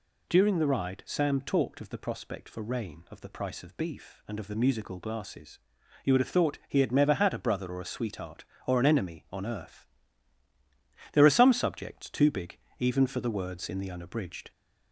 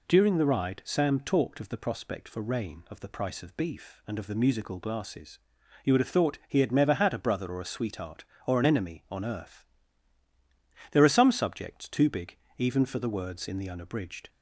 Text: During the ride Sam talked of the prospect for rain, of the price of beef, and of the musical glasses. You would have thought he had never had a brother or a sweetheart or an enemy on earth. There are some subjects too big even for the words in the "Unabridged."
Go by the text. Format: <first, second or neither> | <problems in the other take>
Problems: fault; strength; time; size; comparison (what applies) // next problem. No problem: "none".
second | gets louder; slight; throughout; 2 dB // pauses between "big" and "even"; slight; at 12.5 s; 0.20 s long; slight in the second